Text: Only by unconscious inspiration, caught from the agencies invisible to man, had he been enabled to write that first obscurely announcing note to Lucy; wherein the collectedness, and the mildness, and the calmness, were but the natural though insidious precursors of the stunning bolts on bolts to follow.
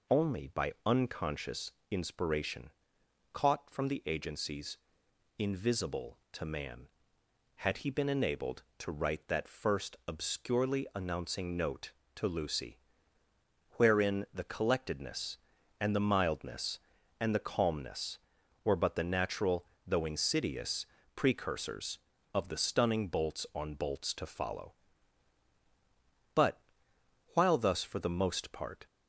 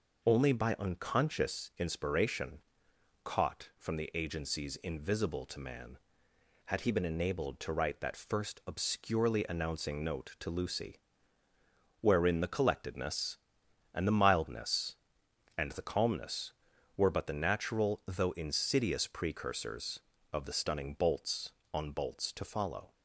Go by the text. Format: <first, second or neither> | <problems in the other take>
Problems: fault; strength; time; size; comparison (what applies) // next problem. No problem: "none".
second | pauses between "unconscious" and "inspiration"; slight; at 1.7 s; 0.18 s long // pauses between "agencies" and "invisible"; noticeable; at 4.7 s; 0.58 s long // pauses between "natural" and "though"; slight; at 19.6 s; 0.22 s long // pauses between "insidious" and "precursors"; slight; at 20.8 s; 0.30 s long // goes on to say "But while thus for the most part"; strong; from 26.3 s on; 2.5 s long